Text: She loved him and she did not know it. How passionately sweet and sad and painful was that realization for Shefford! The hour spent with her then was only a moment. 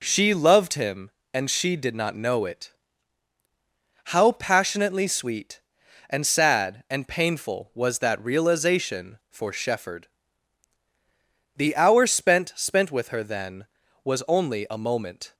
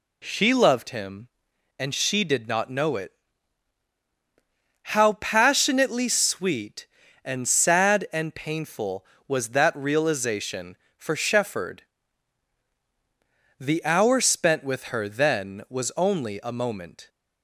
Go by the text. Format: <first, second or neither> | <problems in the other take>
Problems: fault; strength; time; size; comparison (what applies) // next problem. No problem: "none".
second | says "spent" twice; at 12.5 s